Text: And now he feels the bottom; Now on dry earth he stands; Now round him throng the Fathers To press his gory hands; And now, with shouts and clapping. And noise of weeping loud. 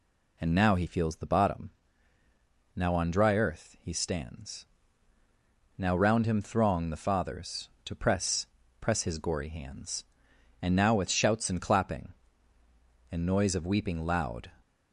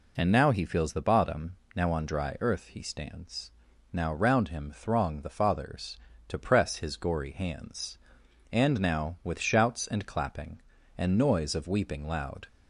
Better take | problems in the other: second | says "press" twice; at 8.7 s

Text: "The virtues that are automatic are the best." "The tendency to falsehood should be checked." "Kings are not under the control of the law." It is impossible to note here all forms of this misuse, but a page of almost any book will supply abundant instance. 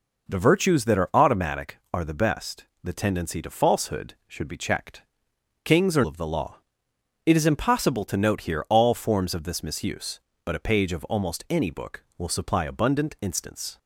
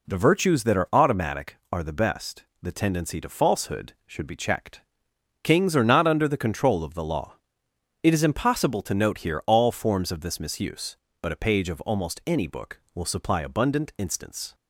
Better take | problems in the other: second | skips "not under the control"; at 6.0 s

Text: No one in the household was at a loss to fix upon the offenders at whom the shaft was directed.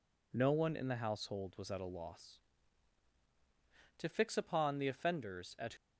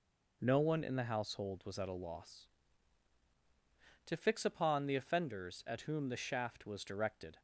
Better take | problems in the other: second | stops before "whom the shaft was directed"; at 5.7 s

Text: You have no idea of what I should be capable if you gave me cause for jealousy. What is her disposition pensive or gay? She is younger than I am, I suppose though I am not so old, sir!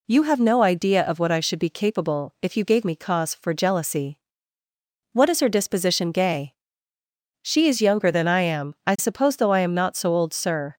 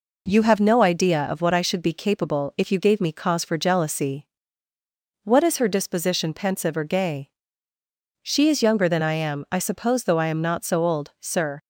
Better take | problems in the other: second | skips "pensive or"; at 6.1 s

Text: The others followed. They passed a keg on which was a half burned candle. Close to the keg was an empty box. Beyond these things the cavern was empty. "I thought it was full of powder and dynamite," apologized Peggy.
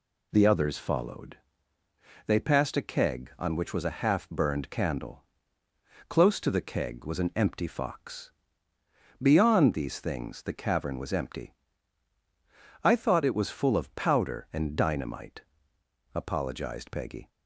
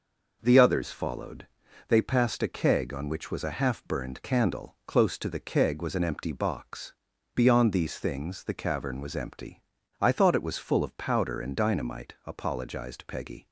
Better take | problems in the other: second | says "fox" for "box"; at 7.6 s

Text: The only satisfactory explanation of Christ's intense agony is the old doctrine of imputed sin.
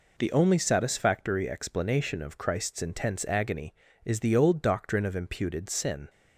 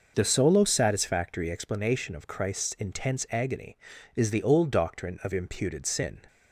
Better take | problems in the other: first | says "solo" for "only"; at 0.2 s

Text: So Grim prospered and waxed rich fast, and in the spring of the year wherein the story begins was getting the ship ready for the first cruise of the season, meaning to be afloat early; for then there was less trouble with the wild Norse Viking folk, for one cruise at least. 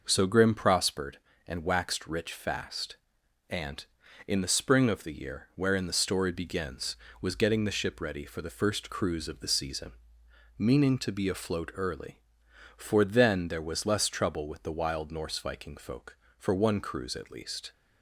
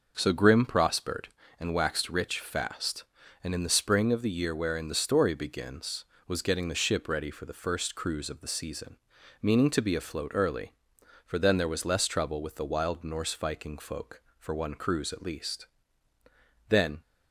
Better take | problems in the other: first | starts louder than the rest; noticeable; until 1.1 s; 6 dB // goes on to say "Then"; slight; from 16.6 s on; 0.30 s long

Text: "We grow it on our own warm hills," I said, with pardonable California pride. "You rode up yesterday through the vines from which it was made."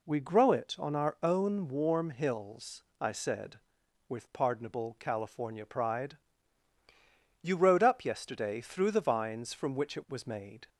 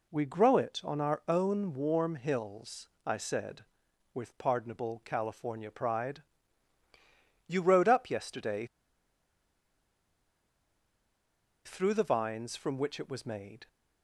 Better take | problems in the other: first | pauses between "yesterday" and "through"; strong; at 8.6 s; 2.9 s long

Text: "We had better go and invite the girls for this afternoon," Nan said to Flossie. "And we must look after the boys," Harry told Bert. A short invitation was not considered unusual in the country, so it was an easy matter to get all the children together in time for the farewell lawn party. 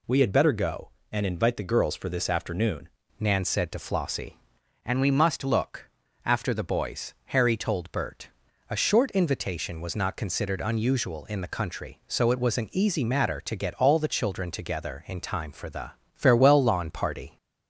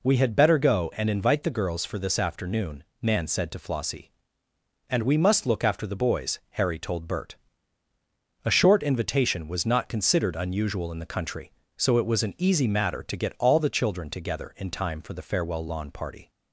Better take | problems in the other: second | changes voice at "Nan"; from 3.1 s on; 14.2 s long // pauses between "look" and "after"; slight; at 5.9 s; 0.34 s long // pauses between "the" and "farewell"; slight; at 15.9 s; 0.24 s long

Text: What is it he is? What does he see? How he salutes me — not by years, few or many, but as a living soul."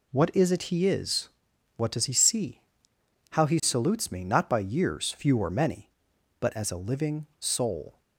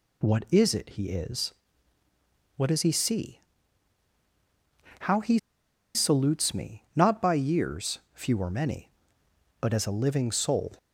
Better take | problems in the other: first | pauses between "he" and "salutes"; noticeable; at 5.3 s; 0.59 s long

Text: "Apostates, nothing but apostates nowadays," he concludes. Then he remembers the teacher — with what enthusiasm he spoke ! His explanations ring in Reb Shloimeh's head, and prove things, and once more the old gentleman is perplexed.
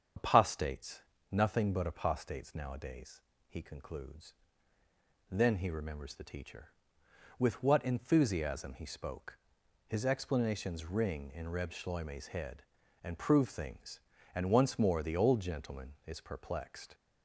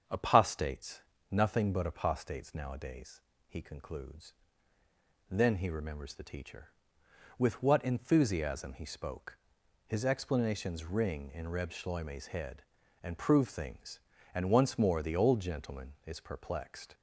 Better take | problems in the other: second | loses the start of "Apostates"; at 0.1 s; 80 ms // starts louder than the rest; strong; until 1.4 s; 7.5 dB; also in the second

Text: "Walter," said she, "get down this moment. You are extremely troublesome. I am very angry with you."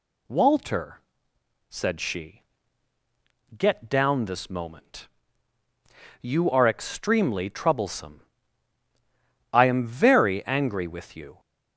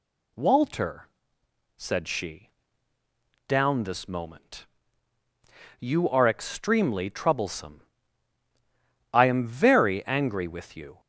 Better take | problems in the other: first | skips "get"; at 2.9 s

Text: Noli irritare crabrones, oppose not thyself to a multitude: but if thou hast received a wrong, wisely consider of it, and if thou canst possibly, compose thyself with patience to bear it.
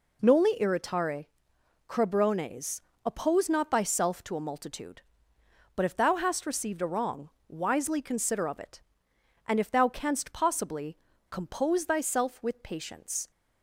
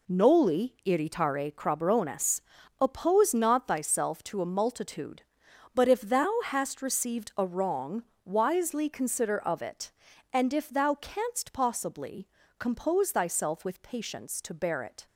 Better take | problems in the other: second | pauses between "irritare" and "crabrones"; noticeable; at 1.2 s; 0.62 s long // stops before "to bear it"; at 13.3 s

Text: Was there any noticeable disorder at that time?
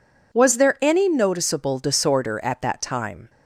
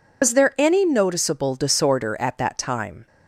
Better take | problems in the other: first | loses the start of "Was"; at 0.2 s; 115 ms

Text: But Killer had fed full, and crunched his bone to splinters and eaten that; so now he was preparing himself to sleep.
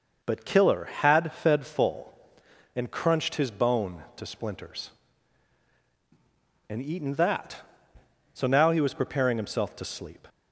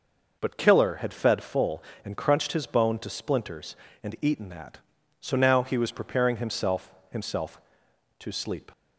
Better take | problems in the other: first | says "himself" twice; at 7.1 s

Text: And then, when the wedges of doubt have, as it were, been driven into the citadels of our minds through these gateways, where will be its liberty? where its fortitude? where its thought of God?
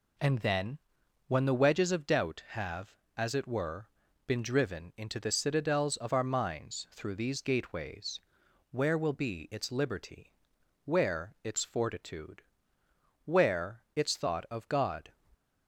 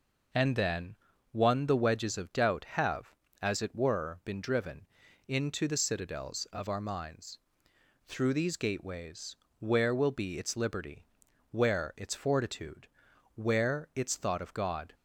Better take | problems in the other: first | says "one" for "when"; at 1.3 s // pauses between "driven" and "into"; at 4.8 s; 0.42 s long // pauses between "minds" and "through"; noticeable; at 7.3 s; 0.68 s long

